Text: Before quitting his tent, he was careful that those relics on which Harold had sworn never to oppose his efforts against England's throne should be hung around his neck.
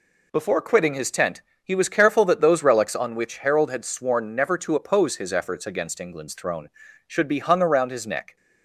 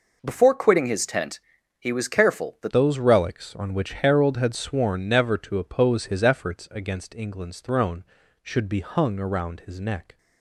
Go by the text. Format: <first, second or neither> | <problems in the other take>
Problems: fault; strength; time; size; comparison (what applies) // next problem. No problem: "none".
first | changes voice at "those"; from 2.6 s on; 7.5 s long